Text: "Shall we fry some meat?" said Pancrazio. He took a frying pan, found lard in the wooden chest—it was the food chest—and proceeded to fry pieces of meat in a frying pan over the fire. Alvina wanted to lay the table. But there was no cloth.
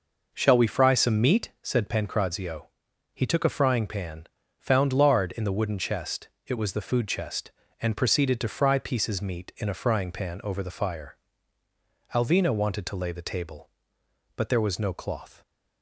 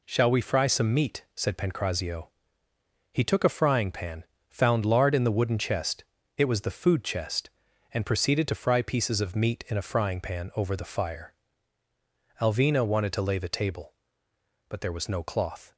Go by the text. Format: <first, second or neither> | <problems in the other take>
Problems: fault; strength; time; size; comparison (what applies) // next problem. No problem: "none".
second | skips "of"; at 9.2 s